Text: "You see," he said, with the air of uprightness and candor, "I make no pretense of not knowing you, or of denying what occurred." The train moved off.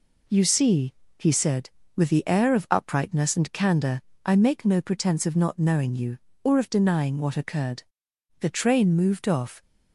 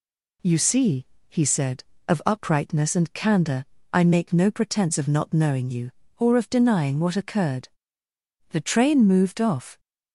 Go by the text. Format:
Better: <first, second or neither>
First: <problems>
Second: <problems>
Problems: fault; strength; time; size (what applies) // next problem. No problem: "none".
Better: first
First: none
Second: skips "with the air"; at 1.9 s